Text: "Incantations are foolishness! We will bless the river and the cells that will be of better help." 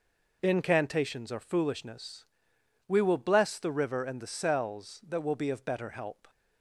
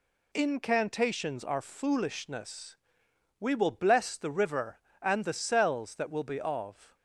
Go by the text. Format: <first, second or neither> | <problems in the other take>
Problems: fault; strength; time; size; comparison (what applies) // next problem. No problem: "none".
first | stops before "better help"; at 6.9 s